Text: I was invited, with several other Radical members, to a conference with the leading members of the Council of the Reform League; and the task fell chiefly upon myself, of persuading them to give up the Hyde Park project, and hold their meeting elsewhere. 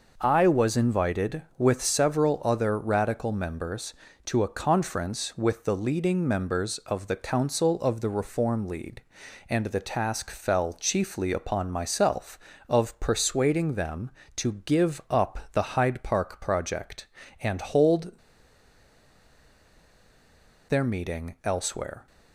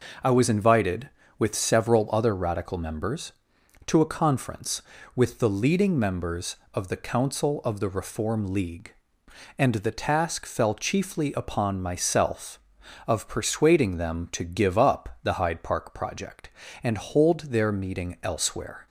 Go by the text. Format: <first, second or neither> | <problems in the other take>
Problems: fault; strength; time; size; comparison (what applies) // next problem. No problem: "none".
second | pauses between "hold" and "their"; strong; at 18.1 s; 2.5 s long